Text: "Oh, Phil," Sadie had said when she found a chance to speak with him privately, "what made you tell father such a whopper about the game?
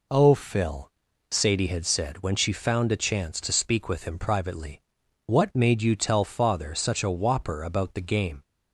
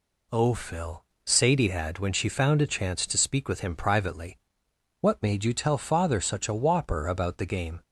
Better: first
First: none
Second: skips "said"; at 1.9 s

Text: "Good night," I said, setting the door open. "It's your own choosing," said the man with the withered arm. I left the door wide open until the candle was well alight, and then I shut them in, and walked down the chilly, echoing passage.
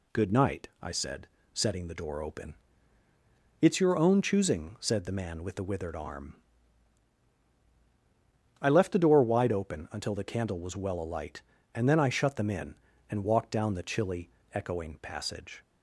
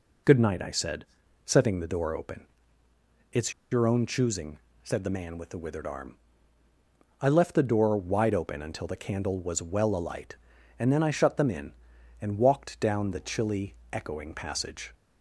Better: first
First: none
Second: pauses between "It's" and "your"; slight; at 3.5 s; 0.18 s long

